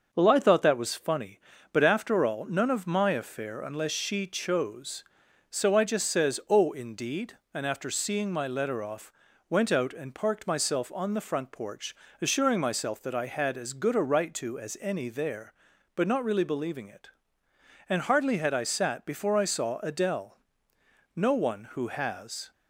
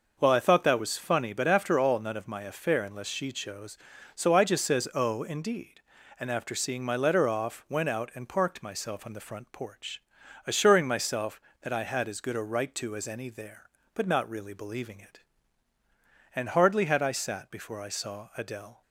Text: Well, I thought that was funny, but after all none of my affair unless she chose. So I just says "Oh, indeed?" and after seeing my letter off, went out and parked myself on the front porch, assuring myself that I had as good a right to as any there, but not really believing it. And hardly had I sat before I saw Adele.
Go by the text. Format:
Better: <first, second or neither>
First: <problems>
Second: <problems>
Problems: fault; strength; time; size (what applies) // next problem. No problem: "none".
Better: second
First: starts louder than the rest; until 1.1 s; 6.5 dB // goes on to say "No one who has"; from 21.1 s on; 1.3 s long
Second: none